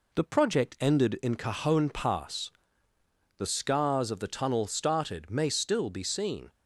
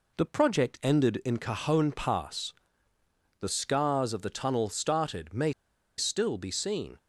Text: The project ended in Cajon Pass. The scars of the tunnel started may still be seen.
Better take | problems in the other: first | pauses between "may" and "still"; noticeable; at 5.5 s; 0.46 s long

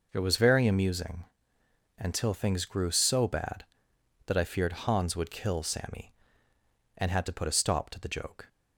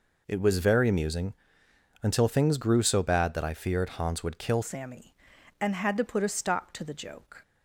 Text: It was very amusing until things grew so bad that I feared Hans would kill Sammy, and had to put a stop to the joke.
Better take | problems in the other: first | pauses between "amusing" and "until"; noticeable; at 1.3 s; 0.68 s long; noticeable in the first // changes voice at "Sammy"; from 4.6 s on; 2.8 s long

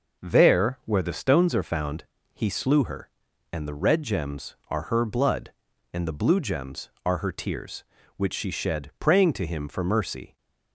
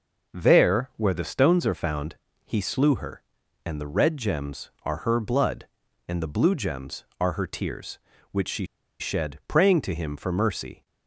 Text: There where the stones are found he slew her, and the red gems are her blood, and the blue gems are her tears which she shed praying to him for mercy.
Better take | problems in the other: first | pauses between "found" and "he"; slight; at 2.1 s; 0.32 s long; slight in the first // pauses between "she" and "shed"; slight; at 8.6 s; 0.34 s long

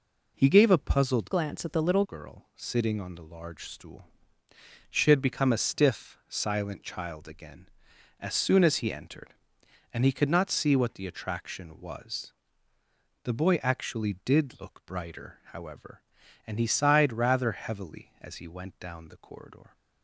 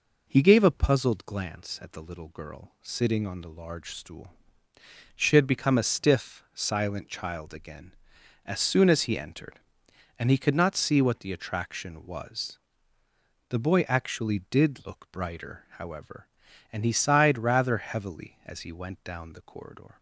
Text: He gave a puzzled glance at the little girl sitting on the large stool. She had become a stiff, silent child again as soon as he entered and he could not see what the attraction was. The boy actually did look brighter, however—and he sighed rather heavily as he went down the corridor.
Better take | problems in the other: second | changes voice from "glance" to "little"; from 1.3 to 2.0 s; 0.7 s long

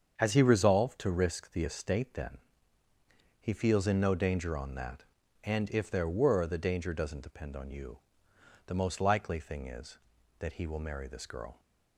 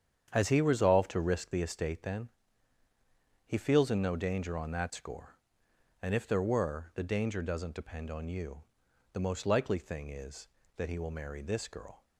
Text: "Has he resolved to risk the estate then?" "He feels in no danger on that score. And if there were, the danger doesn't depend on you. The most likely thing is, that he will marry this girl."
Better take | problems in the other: second | starts louder than the rest; until 1.1 s; 7 dB; strong in the second // skips "score"; at 5.2 s

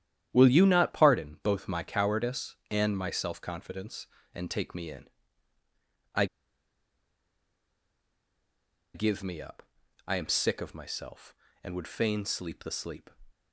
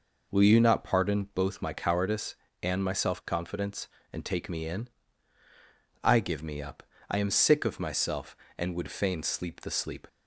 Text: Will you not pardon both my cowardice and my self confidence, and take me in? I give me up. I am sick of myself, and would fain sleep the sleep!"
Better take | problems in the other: second | starts louder than the rest; strong; until 1.3 s; 11 dB // pauses between "I" and "give"; strong; at 6.2 s; 2.6 s long

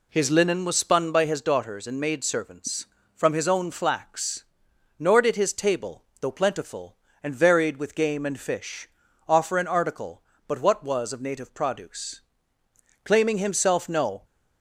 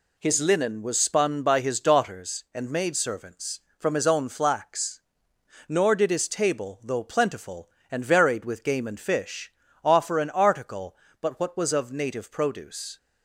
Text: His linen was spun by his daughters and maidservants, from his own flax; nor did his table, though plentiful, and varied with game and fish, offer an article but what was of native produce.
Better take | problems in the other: second | goes on to say "Claiming himself no"; noticeable; from 13.0 s on; 1.2 s long

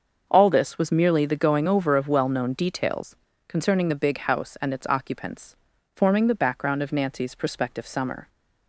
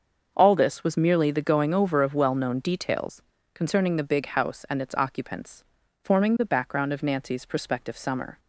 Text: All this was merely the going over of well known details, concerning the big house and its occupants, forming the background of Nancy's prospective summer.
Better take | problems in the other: neither | starts louder than the rest; the same in both

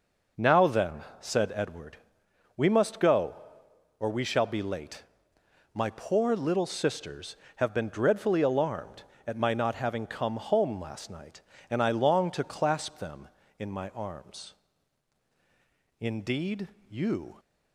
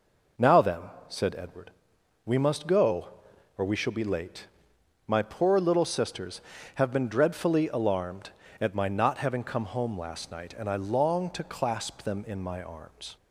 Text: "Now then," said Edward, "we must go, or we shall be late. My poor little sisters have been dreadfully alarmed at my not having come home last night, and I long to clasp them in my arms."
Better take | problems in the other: second | goes on to say "Indeed you"; from 16.0 s on; 1.3 s long

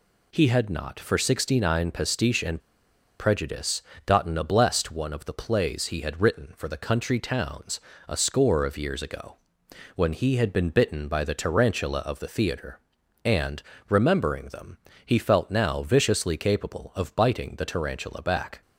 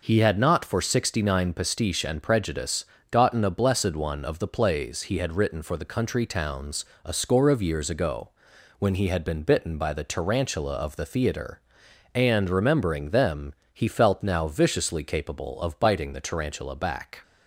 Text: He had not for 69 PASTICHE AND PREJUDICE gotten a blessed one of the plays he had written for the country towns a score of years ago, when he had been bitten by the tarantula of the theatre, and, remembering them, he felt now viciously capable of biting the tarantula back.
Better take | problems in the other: second | pauses between "AND" and "PREJUDICE"; noticeable; at 2.6 s; 0.58 s long // pauses between "PREJUDICE" and "gotten"; slight; at 3.8 s; 0.24 s long; slight in the second // pauses between "towns" and "a"; slight; at 7.7 s; 0.28 s long; slight in the second

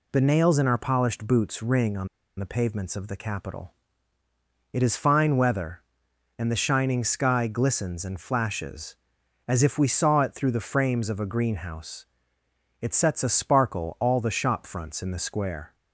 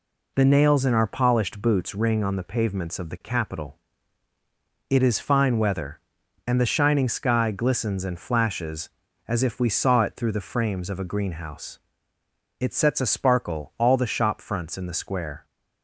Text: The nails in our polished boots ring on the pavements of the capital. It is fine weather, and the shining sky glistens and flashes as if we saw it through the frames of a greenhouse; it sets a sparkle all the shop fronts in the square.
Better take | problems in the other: second | pauses between "on" and "the"; slight; at 2.0 s; 0.31 s long

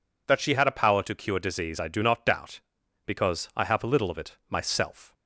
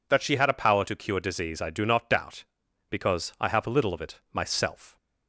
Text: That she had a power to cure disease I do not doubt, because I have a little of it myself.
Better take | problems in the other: neither | none

